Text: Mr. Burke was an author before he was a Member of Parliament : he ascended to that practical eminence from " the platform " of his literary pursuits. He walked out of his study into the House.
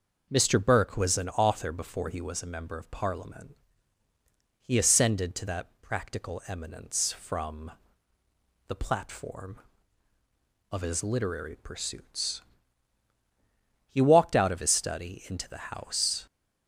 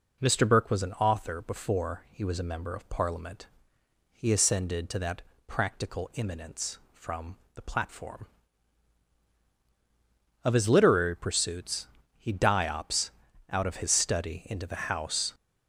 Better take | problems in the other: first | starts louder than the rest; strong; until 1.2 s; 8.5 dB; also in the first // pauses between "that" and "practical"; slight; at 5.2 s; 0.24 s long // says "diops" for "walked"; at 12.3 s

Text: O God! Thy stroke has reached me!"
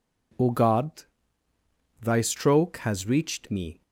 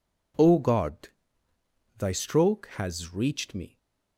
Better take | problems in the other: neither | none

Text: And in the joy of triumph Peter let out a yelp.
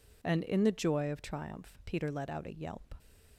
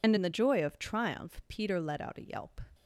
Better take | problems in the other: first | loses the start of "And"; at 0.0 s; 35 ms

